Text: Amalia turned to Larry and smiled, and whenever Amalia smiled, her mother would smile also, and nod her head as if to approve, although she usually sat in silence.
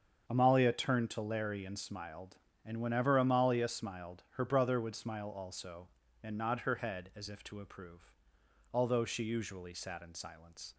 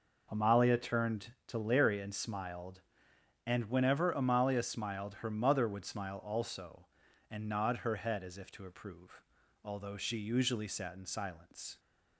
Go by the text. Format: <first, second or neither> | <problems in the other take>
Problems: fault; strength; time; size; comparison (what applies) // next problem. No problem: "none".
second | starts louder than the rest; until 1.2 s; 7 dB // says "brother" for "mother"; at 4.4 s